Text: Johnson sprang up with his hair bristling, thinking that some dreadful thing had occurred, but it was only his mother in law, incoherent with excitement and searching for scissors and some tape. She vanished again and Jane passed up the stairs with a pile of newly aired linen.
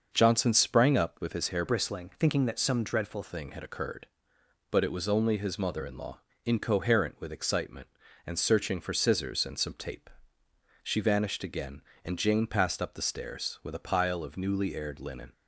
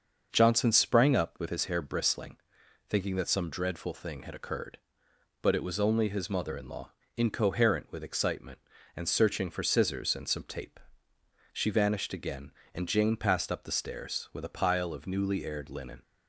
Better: second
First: starts louder than the rest; until 1.1 s; 6 dB // changes voice from "bristling" to "dreadful"; from 1.6 to 3.2 s; 1.6 s long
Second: starts louder than the rest; until 1.3 s; 6.5 dB

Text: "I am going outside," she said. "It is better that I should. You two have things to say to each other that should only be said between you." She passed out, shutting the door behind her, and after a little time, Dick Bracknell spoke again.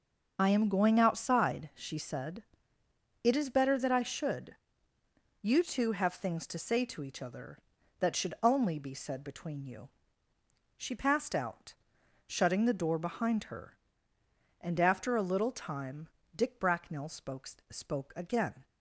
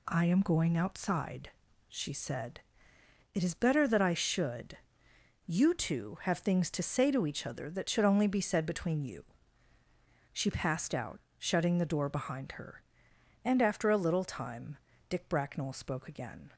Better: second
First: starts louder than the rest; noticeable; until 1.3 s; 6 dB // says "spoke" twice; at 17.6 s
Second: none

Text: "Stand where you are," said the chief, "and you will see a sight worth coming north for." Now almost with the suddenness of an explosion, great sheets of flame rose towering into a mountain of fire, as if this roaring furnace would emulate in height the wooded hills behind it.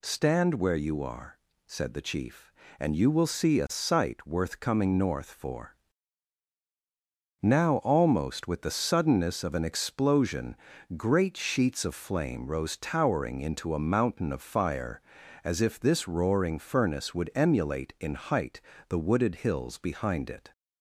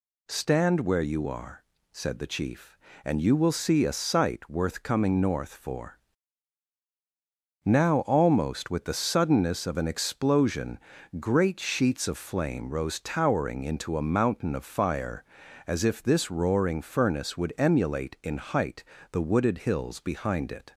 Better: neither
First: pauses between "height" and "the"; slight; at 18.6 s; 0.28 s long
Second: pauses between "height" and "the"; slight; at 18.8 s; 0.28 s long

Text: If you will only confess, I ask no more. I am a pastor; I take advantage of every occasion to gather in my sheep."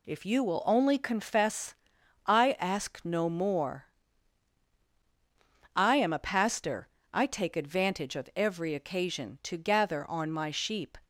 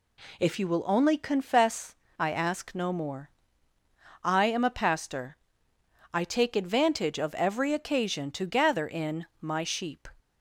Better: second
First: says "on" for "in"; at 10.0 s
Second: none

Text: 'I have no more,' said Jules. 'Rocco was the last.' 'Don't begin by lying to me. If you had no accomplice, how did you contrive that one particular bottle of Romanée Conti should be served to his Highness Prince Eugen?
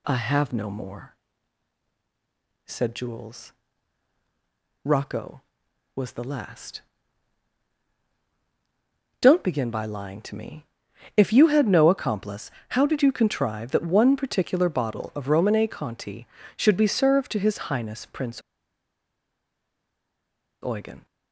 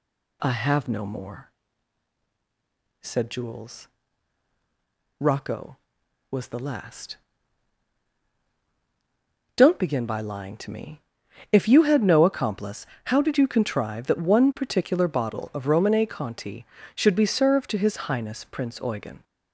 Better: second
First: pauses between "Prince" and "Eugen"; strong; at 18.4 s; 2.2 s long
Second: none

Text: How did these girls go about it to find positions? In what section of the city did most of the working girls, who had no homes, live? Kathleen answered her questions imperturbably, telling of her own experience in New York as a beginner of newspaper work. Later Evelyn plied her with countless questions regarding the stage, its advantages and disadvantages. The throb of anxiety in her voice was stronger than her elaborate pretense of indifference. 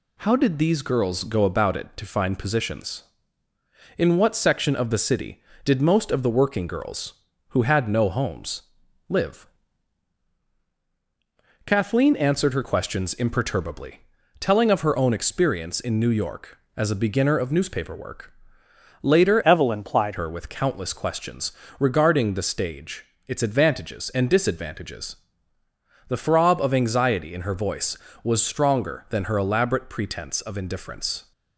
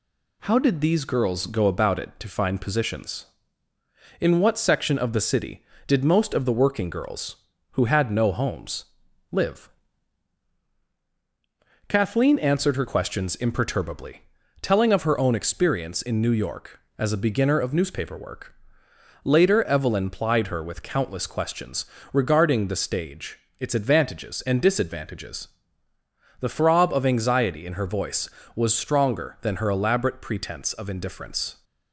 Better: second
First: changes voice from "Evelyn" to "plied"; from 19.4 to 20.1 s; 0.7 s long // pauses between "questions" and "regarding"; slight; at 21.5 s; 0.28 s long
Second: pauses between "questions" and "regarding"; slight; at 21.8 s; 0.28 s long

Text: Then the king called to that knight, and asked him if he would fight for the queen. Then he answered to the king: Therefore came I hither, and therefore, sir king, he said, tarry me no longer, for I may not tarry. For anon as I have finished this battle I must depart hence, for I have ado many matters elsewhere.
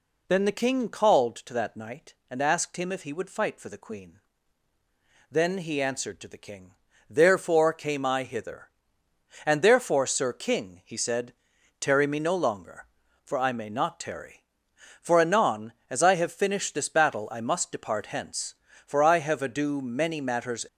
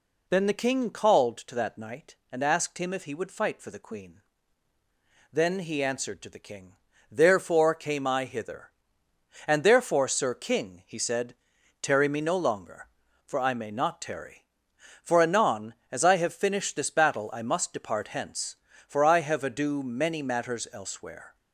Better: second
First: stops before "elsewhere"; at 20.6 s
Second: none

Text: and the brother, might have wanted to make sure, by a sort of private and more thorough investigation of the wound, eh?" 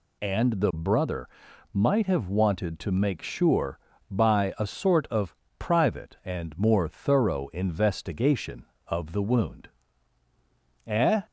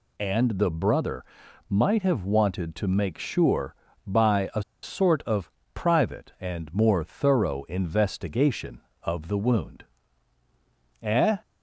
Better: first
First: pauses between "of" and "private"; slight; at 5.3 s; 0.22 s long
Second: pauses between "a" and "sort"; slight; at 4.6 s; 0.20 s long // pauses between "of" and "private"; slight; at 5.5 s; 0.22 s long

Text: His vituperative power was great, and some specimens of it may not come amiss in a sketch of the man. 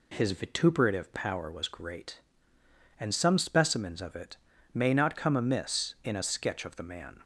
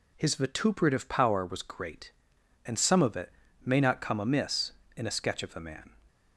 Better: first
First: pauses between "it" and "may"; at 4.3 s; 0.38 s long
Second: skips "specimens"; at 3.0 s // pauses between "it" and "may"; slight; at 3.3 s; 0.34 s long

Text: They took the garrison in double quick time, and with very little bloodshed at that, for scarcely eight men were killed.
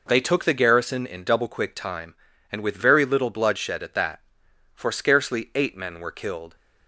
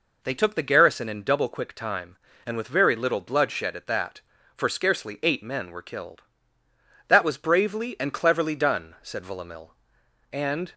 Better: first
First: none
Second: goes on to say "That was bravely and cleverly done said Villamil And"; strong; from 7.0 s on; 3.6 s long

